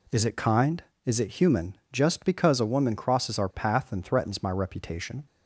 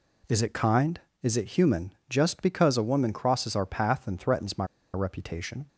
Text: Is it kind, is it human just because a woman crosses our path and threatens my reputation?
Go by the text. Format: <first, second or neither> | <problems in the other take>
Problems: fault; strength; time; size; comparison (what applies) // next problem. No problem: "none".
first | pauses between "human" and "just"; slight; at 1.9 s; 0.18 s long; slight in the first // pauses between "my" and "reputation"; slight; at 4.6 s; 0.29 s long